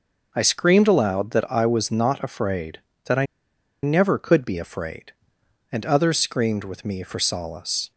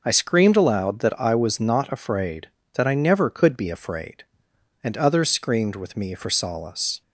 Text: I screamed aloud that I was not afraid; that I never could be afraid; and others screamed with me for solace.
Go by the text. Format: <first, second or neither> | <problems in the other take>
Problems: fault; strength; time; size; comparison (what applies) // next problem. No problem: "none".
second | pauses between "I" and "never"; noticeable; at 3.2 s; 0.57 s long